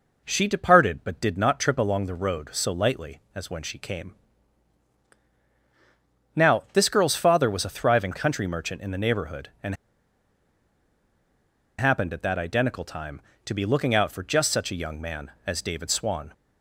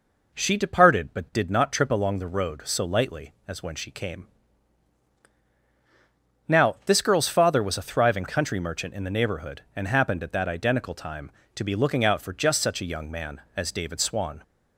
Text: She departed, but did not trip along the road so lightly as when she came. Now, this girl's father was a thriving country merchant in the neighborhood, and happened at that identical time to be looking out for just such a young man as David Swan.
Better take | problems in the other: second | pauses between "and" and "happened"; strong; at 9.7 s; 2.0 s long

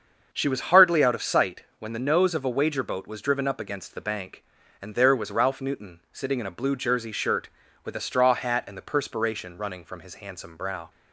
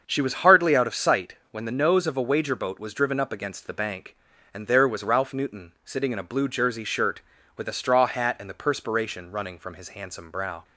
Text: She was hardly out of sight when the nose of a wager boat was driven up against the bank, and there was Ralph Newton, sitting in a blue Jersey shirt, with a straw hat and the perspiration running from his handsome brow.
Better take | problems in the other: neither | starts louder than the rest; the same in both

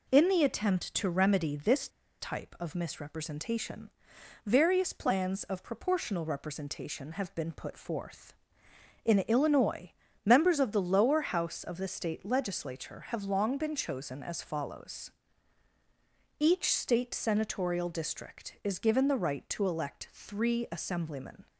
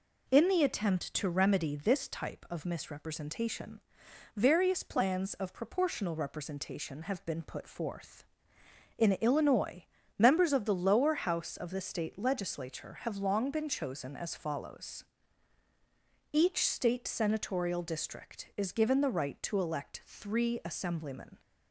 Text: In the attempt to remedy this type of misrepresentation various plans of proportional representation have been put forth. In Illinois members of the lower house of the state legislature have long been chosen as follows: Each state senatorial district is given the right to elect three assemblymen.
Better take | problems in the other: second | pauses between "this" and "type"; slight; at 1.8 s; 0.31 s long // pauses between "misrepresentation" and "various"; noticeable; at 3.8 s; 0.56 s long; noticeable in the second // pauses between "Illinois" and "members"; slight; at 9.9 s; 0.34 s long; slight in the second

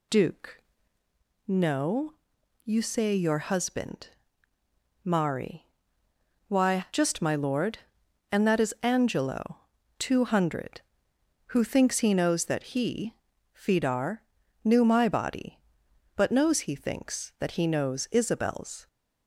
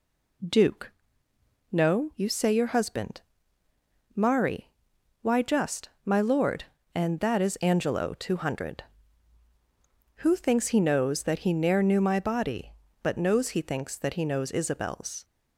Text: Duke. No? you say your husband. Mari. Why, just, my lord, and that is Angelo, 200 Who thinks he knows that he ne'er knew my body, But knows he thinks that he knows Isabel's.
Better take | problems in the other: second | says "fidar" for "ne'er"; at 13.5 s

